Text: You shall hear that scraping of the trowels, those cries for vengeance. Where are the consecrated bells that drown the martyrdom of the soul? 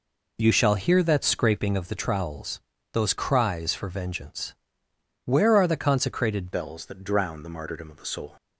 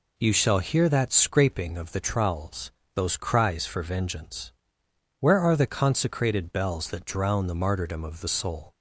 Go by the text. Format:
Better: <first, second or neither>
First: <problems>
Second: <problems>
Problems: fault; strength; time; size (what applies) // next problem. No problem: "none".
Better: second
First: changes voice at "bells"; from 6.5 s on; 1.8 s long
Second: none